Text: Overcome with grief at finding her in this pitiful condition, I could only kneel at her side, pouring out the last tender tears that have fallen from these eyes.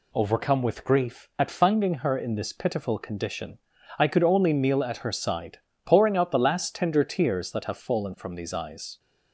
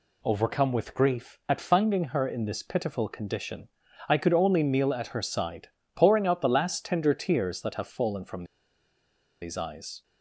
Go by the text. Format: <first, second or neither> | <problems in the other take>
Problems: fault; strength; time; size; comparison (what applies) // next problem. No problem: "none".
first | pauses between "from" and "these"; at 8.4 s; 0.98 s long